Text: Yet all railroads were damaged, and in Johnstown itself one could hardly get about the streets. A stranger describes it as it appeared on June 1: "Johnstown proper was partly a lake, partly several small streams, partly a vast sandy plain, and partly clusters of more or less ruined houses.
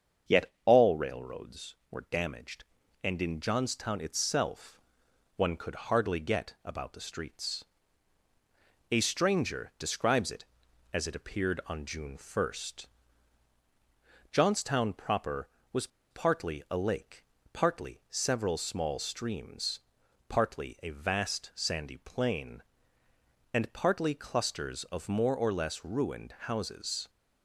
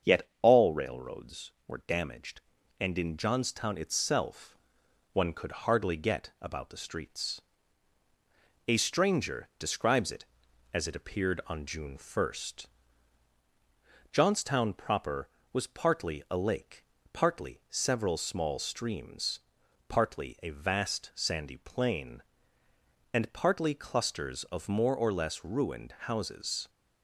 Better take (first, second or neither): second